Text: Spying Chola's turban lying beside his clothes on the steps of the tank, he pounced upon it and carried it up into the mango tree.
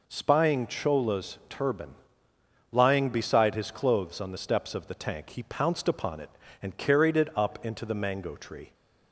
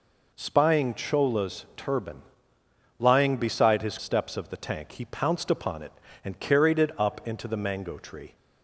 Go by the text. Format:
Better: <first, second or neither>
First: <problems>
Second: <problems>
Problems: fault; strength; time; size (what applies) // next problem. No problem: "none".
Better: first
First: pauses between "turban" and "lying"; noticeable; at 1.9 s; 0.78 s long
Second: pauses between "turban" and "lying"; noticeable; at 2.2 s; 0.78 s long // skips "clothes on the"; at 3.9 s